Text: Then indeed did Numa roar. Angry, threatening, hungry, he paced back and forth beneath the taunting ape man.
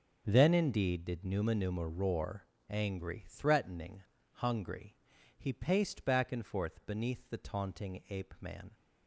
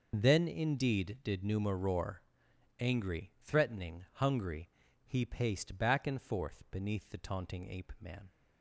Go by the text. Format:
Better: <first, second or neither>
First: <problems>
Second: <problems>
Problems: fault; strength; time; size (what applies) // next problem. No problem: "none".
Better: second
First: starts louder than the rest; until 1.2 s; 6.5 dB // says "Numa" twice; at 1.5 s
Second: none